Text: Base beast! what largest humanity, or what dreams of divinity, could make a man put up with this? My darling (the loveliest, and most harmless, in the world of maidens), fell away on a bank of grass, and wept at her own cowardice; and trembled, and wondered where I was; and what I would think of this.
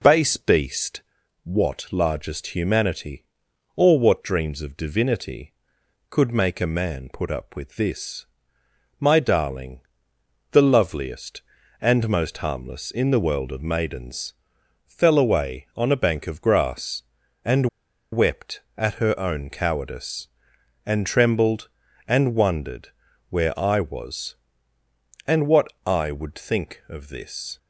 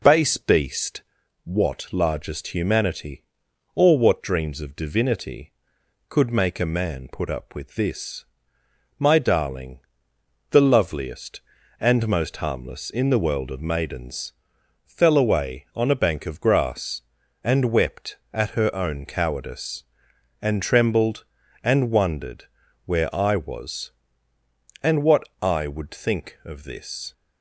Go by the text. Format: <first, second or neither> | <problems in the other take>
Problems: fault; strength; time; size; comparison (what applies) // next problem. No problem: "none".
second | pauses between "and" and "wept"; noticeable; at 17.6 s; 0.45 s long // pauses between "wondered" and "where"; at 22.8 s; 0.40 s long; also in the second // pauses between "what" and "I"; slight; at 25.6 s; 0.22 s long; slight in the second